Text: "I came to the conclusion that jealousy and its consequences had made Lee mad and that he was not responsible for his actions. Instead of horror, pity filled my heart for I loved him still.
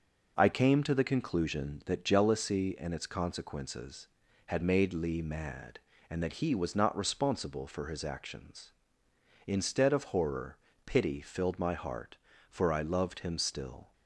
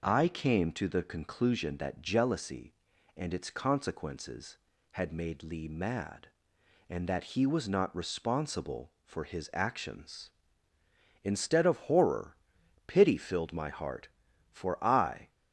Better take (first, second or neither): first